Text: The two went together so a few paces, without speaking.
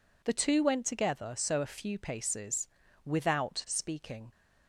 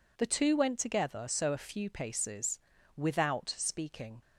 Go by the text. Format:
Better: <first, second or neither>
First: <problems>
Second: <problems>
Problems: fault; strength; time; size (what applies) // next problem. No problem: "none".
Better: neither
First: none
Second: none